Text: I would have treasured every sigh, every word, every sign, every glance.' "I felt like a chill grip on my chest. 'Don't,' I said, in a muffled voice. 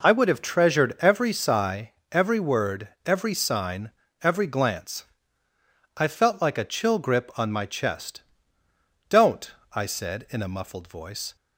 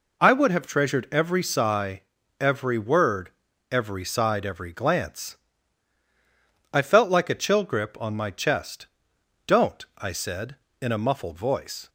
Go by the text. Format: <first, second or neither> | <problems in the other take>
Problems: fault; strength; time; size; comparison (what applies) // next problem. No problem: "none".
first | says "side" for "sign"; at 4.0 s